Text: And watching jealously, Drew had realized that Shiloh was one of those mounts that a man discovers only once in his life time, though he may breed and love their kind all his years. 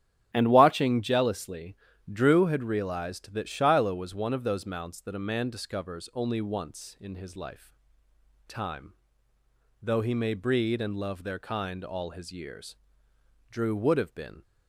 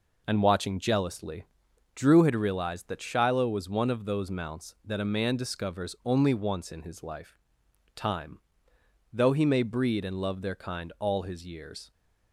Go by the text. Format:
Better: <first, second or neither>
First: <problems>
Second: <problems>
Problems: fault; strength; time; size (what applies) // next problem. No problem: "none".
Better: second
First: starts louder than the rest; strong; until 1.3 s; 10.5 dB // pauses between "life" and "time"; noticeable; at 7.6 s; 0.80 s long // goes on to say "Drew would have been"; noticeable; from 13.4 s on; 0.92 s long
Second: pauses between "life" and "time"; noticeable; at 7.3 s; 0.56 s long